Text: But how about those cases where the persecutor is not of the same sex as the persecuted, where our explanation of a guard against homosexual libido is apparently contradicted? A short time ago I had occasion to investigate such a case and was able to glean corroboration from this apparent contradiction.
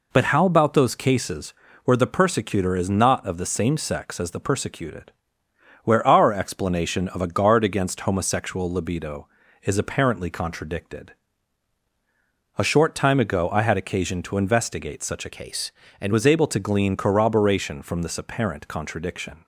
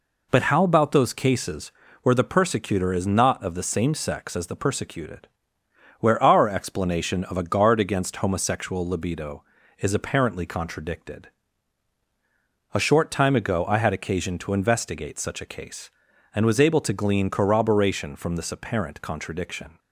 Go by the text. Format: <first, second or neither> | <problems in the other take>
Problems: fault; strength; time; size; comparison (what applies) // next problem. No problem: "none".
second | pauses between "cases" and "where"; slight; at 1.5 s; 0.32 s long; slight in the second // changes voice from "case" to "and"; from 15.3 to 16.1 s; 0.8 s long